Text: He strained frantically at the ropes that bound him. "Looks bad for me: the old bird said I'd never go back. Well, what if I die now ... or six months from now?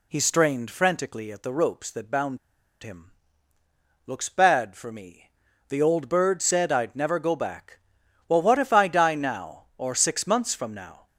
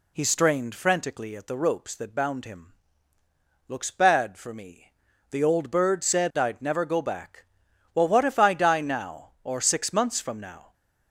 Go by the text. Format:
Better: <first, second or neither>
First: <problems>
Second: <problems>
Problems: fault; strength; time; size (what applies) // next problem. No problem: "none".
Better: second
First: pauses between "bound" and "him"; at 2.3 s; 0.44 s long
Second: none